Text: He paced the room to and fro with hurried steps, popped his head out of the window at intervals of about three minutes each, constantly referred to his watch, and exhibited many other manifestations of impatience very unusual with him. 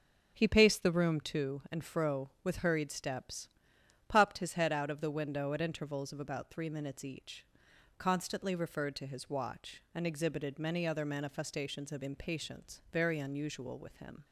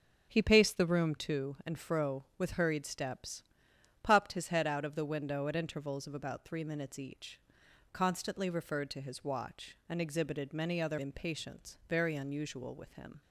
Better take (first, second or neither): first